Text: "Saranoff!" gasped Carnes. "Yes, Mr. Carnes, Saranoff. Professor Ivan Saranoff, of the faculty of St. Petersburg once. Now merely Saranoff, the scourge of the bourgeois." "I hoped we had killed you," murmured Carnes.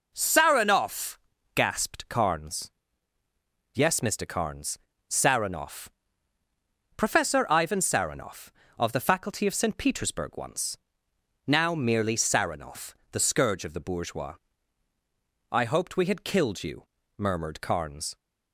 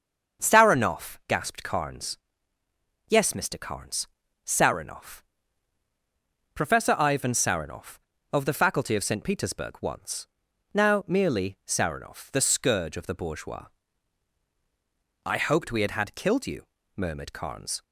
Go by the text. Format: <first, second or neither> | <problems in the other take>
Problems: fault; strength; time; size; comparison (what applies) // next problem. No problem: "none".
first | starts louder than the rest; until 1.4 s; 6.5 dB // says "had" twice; at 15.9 s